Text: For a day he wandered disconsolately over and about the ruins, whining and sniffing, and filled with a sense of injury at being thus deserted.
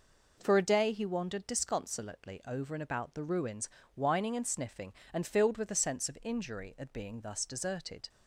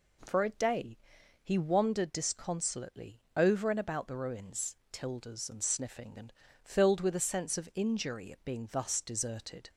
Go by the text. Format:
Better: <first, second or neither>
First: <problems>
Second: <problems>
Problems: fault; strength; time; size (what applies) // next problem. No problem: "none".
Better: first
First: none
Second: pauses between "day" and "he"; at 0.9 s; 0.44 s long // says "tildes" for "whining"; at 4.9 s // pauses between "and" and "filled"; slight; at 6.3 s; 0.32 s long